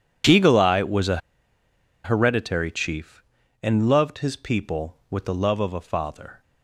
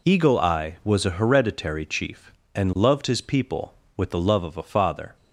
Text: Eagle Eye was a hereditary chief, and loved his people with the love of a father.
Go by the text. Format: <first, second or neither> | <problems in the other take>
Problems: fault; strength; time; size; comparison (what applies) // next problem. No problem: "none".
second | pauses between "a" and "hereditary"; noticeable; at 1.1 s; 0.86 s long